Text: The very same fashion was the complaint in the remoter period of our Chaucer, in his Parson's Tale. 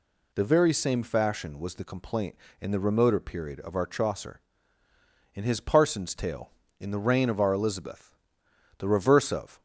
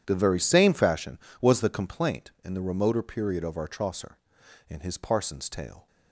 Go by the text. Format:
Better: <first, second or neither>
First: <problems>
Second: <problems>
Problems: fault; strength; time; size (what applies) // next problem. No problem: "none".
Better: second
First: goes on to say "In the reign of our Elizabeth the reverse of"; strong; from 6.8 s on; 2.8 s long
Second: none